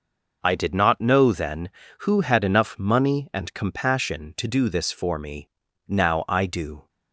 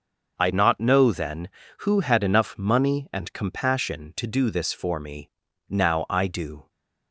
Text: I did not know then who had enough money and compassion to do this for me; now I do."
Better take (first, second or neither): first